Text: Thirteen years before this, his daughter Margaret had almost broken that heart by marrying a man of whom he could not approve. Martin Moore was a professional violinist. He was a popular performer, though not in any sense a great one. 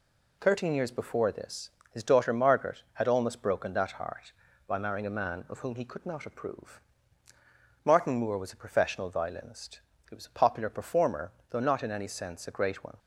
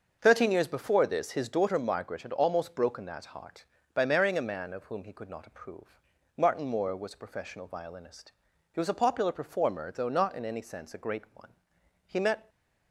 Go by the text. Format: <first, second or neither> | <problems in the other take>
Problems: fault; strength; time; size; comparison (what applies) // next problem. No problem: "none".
first | starts louder than the rest; until 1.2 s; 6.5 dB // goes on to say "He met"; slight; from 12.0 s on; 0.42 s long